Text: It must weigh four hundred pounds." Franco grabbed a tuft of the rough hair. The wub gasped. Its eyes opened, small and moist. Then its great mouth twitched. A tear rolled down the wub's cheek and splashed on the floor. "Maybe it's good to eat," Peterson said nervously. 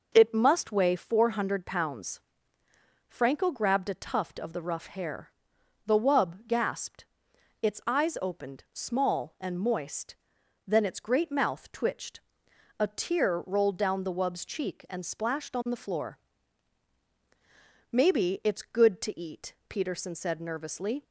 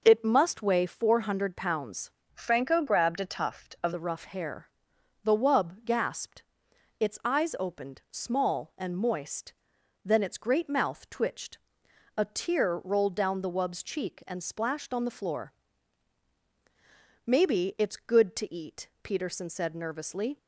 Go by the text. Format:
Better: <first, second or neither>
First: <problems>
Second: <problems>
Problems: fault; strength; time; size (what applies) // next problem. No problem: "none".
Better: first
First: none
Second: changes voice from "Franco" to "of"; from 2.3 to 3.9 s; 1.6 s long